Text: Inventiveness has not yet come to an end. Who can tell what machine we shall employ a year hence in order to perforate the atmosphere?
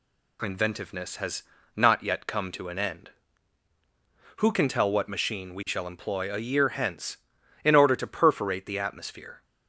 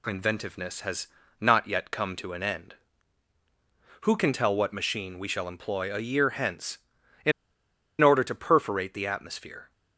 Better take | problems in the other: first | pauses between "has" and "not"; slight; at 1.0 s; 0.34 s long; slight in the first // pauses between "in" and "order"; noticeable; at 7.3 s; 0.70 s long

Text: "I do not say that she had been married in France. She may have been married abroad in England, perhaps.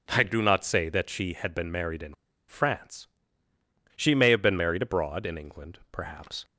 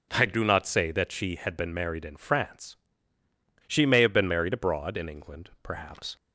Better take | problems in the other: second | pauses between "in" and "France"; slight; at 2.1 s; 0.35 s long

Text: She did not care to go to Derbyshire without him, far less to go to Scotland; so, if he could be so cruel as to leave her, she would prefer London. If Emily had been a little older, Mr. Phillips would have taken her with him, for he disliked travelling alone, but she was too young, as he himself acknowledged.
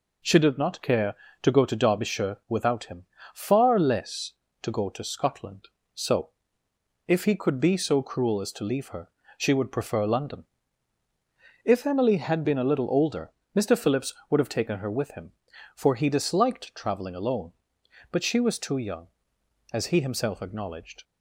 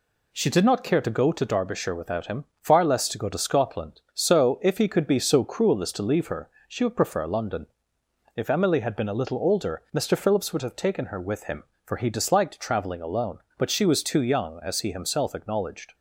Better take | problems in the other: neither | none

